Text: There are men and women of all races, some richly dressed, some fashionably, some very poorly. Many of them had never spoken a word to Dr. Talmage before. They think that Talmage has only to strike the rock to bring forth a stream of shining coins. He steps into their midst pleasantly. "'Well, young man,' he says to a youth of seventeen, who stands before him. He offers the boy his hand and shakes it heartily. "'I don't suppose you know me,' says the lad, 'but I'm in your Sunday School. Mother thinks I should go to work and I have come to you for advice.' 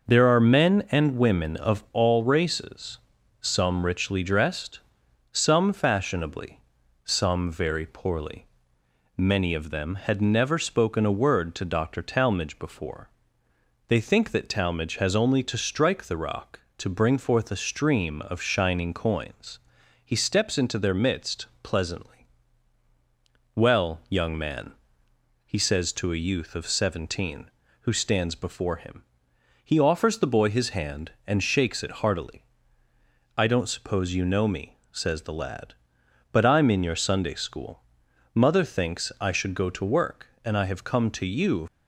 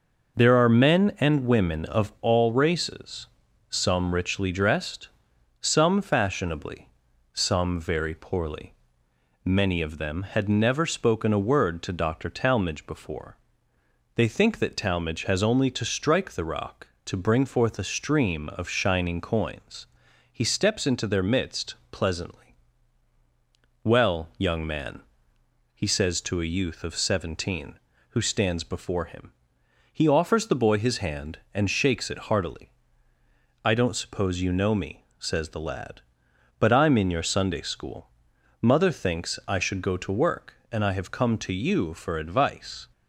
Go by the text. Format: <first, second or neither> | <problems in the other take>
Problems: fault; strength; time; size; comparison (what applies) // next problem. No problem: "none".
second | pauses between "midst" and "pleasantly"; slight; at 21.4 s; 0.16 s long; slight in the second // stops before "for advice"; at 41.6 s